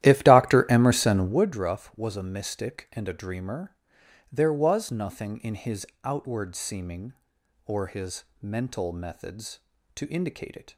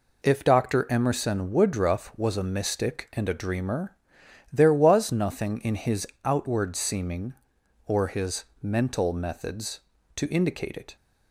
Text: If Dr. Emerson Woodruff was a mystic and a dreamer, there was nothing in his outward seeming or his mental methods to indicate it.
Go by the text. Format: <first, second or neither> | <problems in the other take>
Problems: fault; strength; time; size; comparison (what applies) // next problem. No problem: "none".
second | starts louder than the rest; strong; until 1.5 s; 13.5 dB // pauses between "his" and "outward"; slight; at 5.8 s; 0.18 s long; slight in the second // pauses between "his" and "mental"; slight; at 8.2 s; 0.18 s long; slight in the second